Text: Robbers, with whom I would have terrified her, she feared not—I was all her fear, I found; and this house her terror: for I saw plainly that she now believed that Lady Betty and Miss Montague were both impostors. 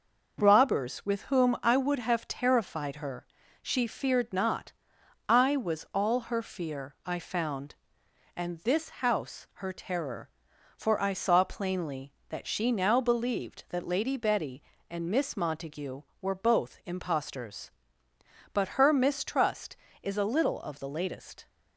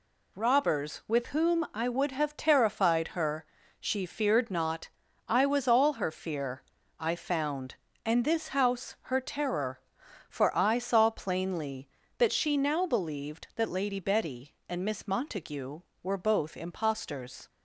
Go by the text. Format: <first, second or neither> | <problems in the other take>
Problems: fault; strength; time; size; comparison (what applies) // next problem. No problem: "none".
second | goes on to say "But her mistrust is a little of the latest"; strong; from 18.5 s on; 2.9 s long